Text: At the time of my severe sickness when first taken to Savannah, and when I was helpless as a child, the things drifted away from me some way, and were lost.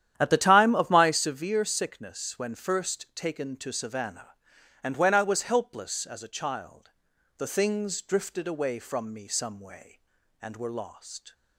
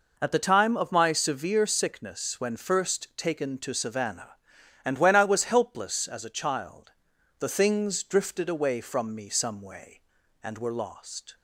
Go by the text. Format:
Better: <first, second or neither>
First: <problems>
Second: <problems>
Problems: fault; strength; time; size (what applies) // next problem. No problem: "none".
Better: second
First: starts louder than the rest; strong; until 1.3 s; 10.5 dB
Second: none